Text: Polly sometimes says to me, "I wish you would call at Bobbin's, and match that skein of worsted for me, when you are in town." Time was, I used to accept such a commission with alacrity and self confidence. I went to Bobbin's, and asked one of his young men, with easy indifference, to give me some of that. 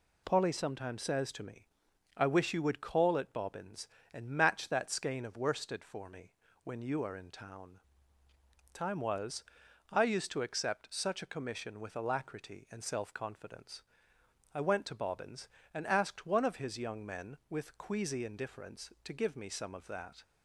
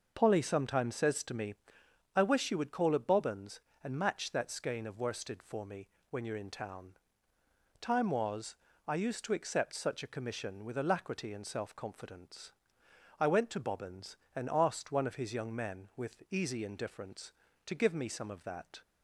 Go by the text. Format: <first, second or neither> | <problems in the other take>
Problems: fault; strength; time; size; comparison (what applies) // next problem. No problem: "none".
second | says "queasy" for "easy"; at 17.7 s